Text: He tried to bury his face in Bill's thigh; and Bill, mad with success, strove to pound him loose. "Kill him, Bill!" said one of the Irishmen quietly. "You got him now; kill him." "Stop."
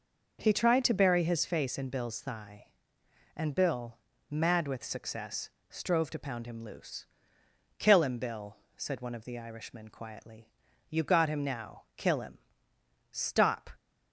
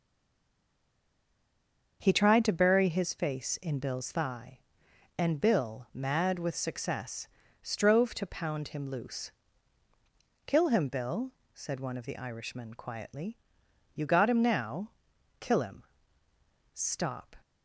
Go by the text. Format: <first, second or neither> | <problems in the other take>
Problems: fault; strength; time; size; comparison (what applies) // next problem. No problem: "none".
first | stays silent before the first word; noticeable; until 2.0 s; 2.0 s long // starts louder than the rest; until 3.0 s; 6.5 dB